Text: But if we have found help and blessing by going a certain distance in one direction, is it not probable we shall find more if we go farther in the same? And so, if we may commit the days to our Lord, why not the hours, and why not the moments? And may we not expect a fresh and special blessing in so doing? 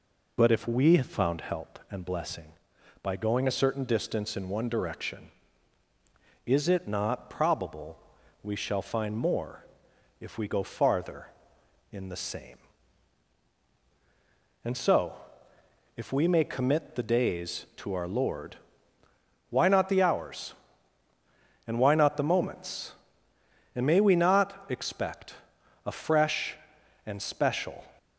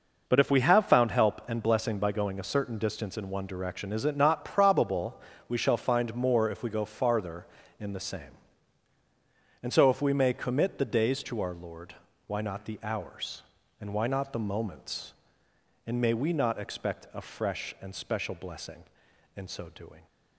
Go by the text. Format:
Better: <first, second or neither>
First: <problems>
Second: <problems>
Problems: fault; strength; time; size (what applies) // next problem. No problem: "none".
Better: second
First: pauses between "probable" and "we"; at 7.9 s; 0.42 s long // pauses between "more" and "if"; noticeable; at 9.6 s; 0.56 s long // pauses between "expect" and "a"; noticeable; at 25.3 s; 0.50 s long // stops before "blessing in so doing"; at 27.9 s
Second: pauses between "probable" and "we"; slight; at 5.1 s; 0.28 s long